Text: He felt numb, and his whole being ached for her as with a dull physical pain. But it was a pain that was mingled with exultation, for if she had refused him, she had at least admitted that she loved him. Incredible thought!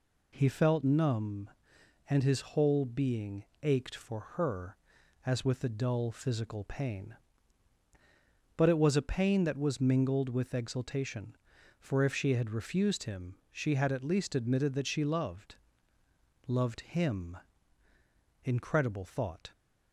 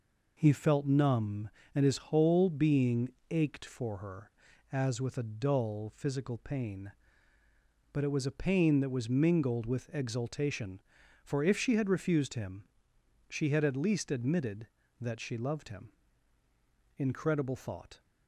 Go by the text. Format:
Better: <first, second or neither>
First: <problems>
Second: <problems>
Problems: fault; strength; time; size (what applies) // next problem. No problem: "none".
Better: second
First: pauses between "being" and "ached"; slight; at 3.4 s; 0.18 s long // says "loved" twice; at 16.4 s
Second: pauses between "being" and "ached"; slight; at 3.1 s; 0.16 s long